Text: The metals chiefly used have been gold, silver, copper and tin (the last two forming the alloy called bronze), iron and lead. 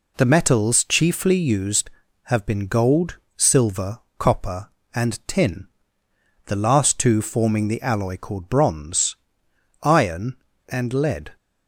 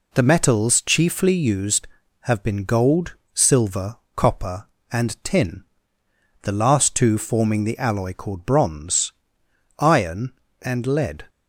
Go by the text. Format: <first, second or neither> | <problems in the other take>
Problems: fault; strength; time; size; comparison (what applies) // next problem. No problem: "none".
neither | none